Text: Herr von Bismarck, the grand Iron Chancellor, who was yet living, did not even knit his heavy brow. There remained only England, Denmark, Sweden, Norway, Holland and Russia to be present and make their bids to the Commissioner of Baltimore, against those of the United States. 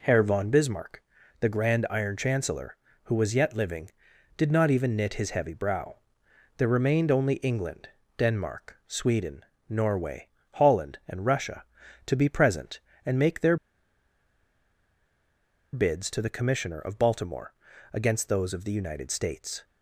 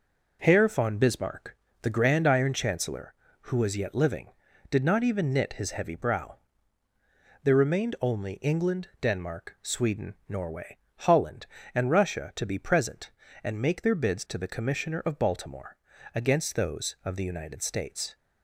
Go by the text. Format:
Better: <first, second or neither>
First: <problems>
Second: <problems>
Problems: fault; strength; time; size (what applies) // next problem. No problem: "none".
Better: second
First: pauses between "their" and "bids"; strong; at 13.5 s; 2.1 s long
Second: none